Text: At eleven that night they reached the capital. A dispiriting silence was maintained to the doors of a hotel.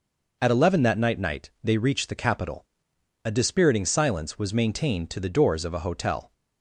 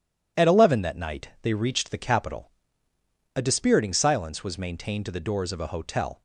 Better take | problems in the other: second | says "night" twice; at 1.1 s

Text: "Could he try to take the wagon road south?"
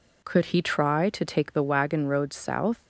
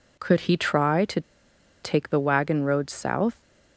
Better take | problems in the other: first | pauses between "to" and "take"; noticeable; at 1.2 s; 0.62 s long

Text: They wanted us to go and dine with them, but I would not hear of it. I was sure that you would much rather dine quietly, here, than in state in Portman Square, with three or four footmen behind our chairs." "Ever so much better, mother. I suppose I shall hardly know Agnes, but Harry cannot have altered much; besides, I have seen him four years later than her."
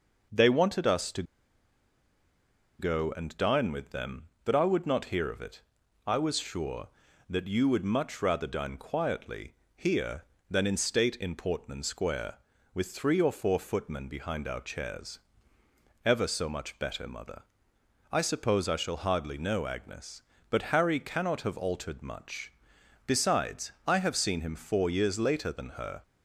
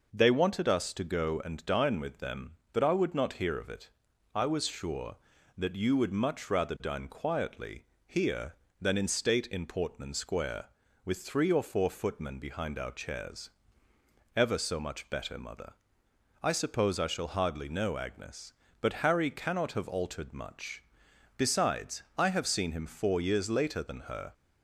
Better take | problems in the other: second | pauses between "to" and "go"; strong; at 1.2 s; 1.5 s long

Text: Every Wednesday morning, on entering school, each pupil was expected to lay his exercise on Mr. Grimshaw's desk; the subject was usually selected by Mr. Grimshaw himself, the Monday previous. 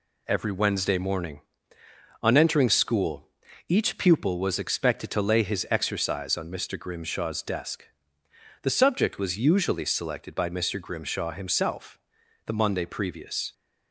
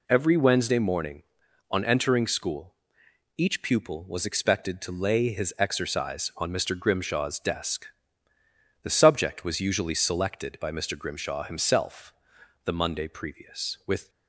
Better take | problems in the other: first | goes on to say "With"; slight; from 13.8 s on; 0.22 s long

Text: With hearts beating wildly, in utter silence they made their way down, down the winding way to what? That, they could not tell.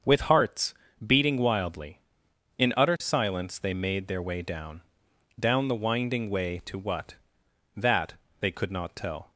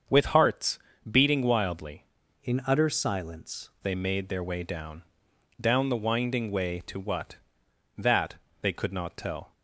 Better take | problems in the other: first | starts louder than the rest; until 1.4 s; 7 dB; also in the first // pauses between "hearts" and "beating"; slight; at 0.7 s; 0.32 s long; slight in the first // changes voice from "in" to "silence"; from 2.4 to 3.6 s; 1.2 s long

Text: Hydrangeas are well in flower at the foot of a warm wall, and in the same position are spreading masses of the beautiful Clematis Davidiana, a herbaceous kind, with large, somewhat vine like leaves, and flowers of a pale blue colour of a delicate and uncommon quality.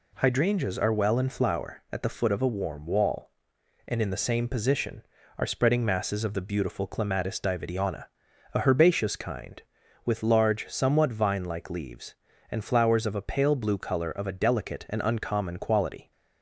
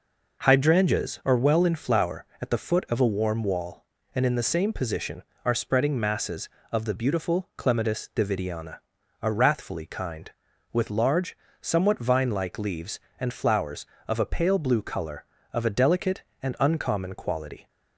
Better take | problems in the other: first | says "wrathfully" for "herbaceous"; at 9.3 s

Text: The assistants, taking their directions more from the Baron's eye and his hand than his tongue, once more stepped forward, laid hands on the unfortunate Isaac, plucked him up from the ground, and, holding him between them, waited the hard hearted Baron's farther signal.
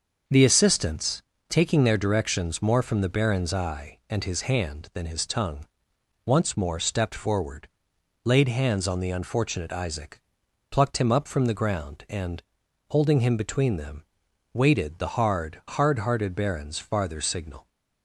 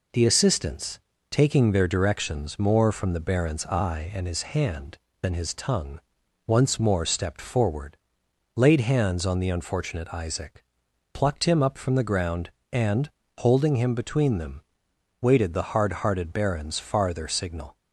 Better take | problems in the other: second | starts louder than the rest; until 1.5 s; 6 dB // says "hard" twice; at 15.6 s

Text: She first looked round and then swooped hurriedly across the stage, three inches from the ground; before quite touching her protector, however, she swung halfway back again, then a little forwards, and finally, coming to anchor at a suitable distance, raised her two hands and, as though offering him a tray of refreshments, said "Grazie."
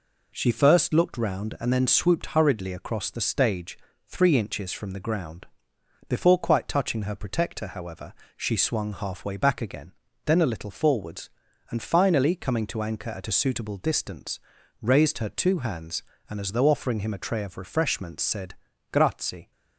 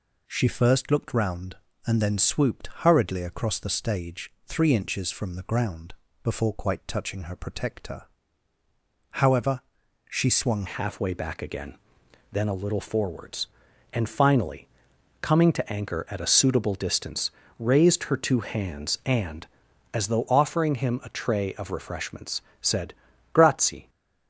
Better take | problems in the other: first | changes voice at "halfway"; from 10.6 s on; 13.2 s long // pauses between "said" and "Grazie"; at 22.9 s; 0.40 s long; slight in the first

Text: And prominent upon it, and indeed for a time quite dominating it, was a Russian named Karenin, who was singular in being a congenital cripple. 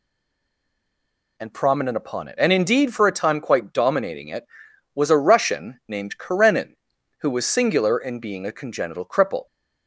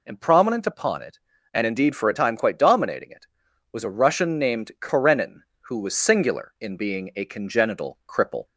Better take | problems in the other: second | stays silent before the first word; noticeable; until 1.3 s; 1.3 s long

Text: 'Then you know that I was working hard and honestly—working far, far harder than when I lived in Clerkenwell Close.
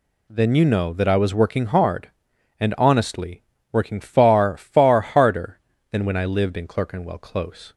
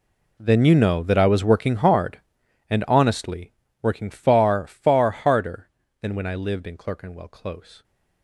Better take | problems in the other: first | gets quieter; strong; throughout; 19.5 dB

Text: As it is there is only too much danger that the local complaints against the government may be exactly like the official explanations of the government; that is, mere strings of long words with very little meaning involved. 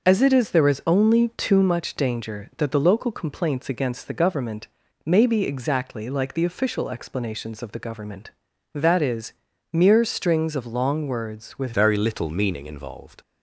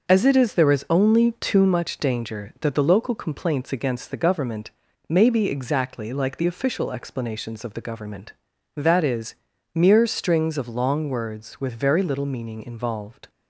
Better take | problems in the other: second | pauses between "government" and "may"; at 4.6 s; 0.38 s long; also in the second // changes voice at "very"; from 11.7 s on; 1.5 s long

